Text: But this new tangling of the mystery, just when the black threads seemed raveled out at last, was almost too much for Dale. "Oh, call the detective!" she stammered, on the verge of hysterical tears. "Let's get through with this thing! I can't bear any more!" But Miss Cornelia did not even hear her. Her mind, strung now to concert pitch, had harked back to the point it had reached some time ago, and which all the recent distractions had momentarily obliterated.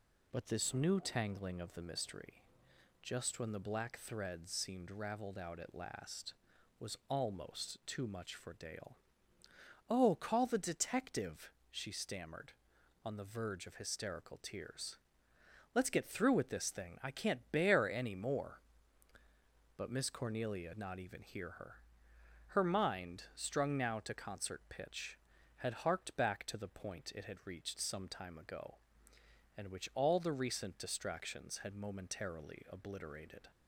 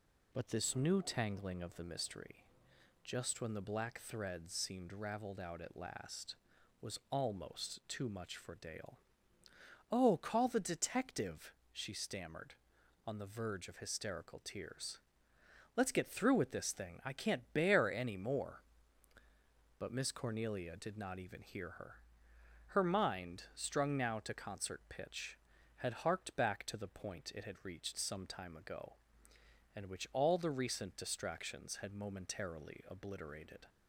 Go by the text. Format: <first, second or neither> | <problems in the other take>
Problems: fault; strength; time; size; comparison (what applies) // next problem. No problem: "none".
second | skips "did"; at 20.7 s